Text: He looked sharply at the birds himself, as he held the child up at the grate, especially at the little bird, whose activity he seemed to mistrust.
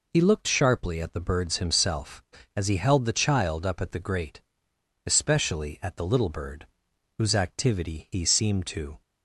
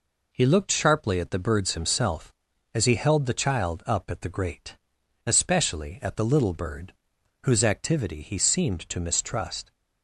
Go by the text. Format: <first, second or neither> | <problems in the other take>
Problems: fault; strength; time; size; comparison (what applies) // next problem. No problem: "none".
second | stops before "mistrust"; at 9.0 s